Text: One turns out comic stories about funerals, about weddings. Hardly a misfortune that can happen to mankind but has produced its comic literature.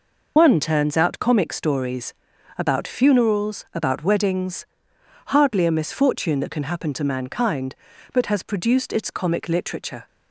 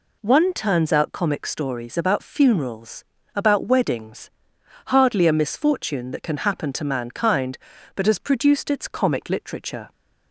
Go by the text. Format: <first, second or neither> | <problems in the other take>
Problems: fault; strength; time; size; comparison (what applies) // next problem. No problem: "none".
second | loses the start of "One"; at 0.3 s; 80 ms // pauses between "stories" and "about"; noticeable; at 2.1 s; 0.46 s long